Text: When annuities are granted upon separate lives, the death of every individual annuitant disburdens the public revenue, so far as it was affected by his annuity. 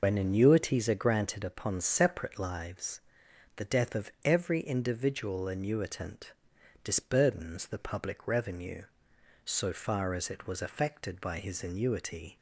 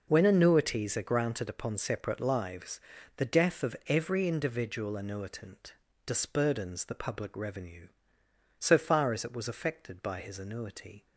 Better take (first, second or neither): second